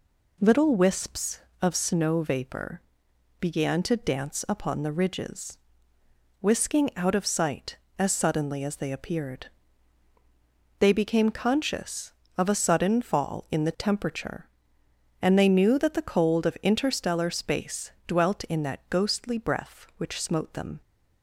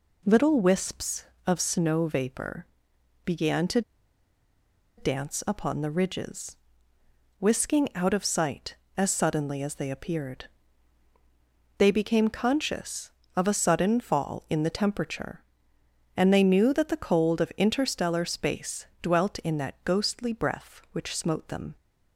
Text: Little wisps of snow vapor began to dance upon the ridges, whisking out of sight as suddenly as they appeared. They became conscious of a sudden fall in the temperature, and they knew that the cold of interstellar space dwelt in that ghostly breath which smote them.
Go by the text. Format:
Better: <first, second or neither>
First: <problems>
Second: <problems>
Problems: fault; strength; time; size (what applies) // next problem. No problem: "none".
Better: first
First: pauses between "vapor" and "began"; noticeable; at 2.7 s; 0.62 s long // pauses between "space" and "dwelt"; slight; at 17.9 s; 0.16 s long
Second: pauses between "vapor" and "began"; noticeable; at 2.6 s; 0.62 s long // pauses between "to" and "dance"; at 3.8 s; 1.1 s long // pauses between "space" and "dwelt"; slight; at 18.8 s; 0.16 s long